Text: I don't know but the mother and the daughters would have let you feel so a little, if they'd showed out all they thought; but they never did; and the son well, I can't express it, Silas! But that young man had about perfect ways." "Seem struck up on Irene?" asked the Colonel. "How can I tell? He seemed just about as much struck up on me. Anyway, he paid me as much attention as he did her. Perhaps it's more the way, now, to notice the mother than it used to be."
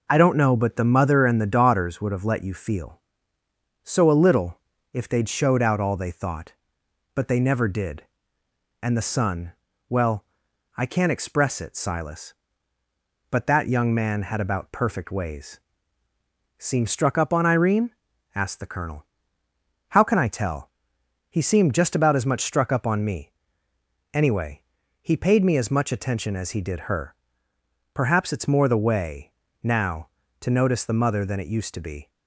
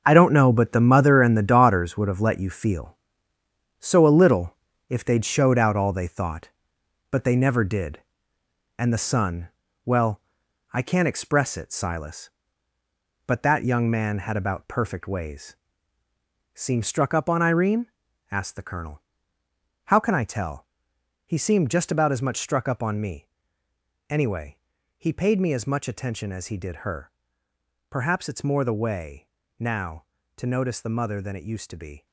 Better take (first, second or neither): first